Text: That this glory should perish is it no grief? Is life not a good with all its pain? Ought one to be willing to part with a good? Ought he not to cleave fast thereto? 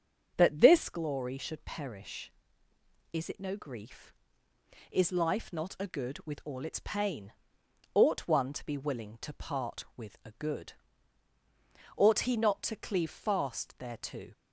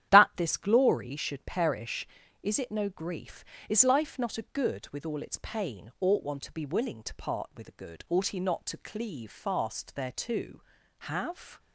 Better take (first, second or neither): first